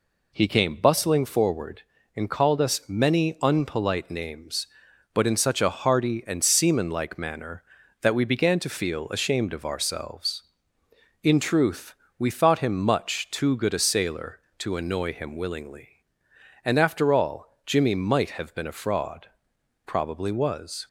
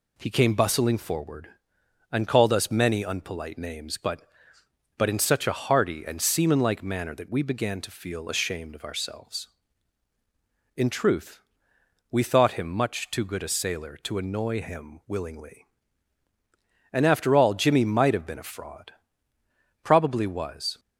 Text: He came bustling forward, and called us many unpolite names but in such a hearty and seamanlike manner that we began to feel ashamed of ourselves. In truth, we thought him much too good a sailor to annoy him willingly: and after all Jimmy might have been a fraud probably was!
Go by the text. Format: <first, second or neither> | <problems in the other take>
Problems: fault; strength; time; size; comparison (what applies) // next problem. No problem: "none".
first | says "but" twice; at 4.9 s // pauses between "fraud" and "probably"; noticeable; at 18.9 s; 0.90 s long; noticeable in the first